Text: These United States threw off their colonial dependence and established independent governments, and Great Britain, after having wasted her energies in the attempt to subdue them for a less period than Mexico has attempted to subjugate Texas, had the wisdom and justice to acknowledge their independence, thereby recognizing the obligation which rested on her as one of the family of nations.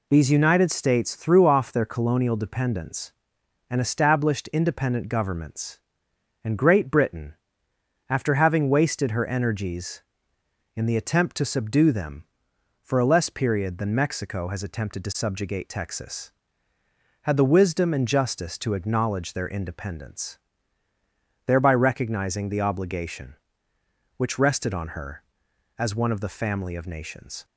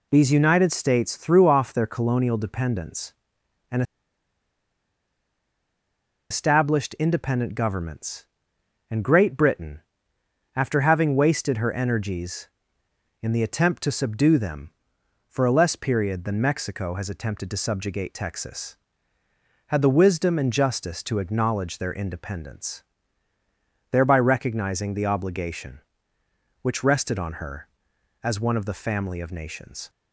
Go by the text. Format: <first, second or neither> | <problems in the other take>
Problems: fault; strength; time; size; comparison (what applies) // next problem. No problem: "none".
first | pauses between "and" and "established"; strong; at 3.8 s; 2.4 s long